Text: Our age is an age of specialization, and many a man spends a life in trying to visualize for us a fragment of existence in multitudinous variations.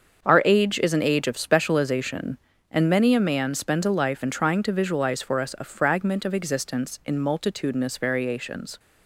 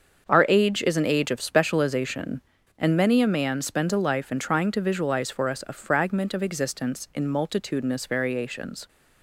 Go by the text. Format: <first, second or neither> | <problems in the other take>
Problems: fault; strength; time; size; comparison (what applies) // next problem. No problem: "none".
neither | starts louder than the rest; the same in both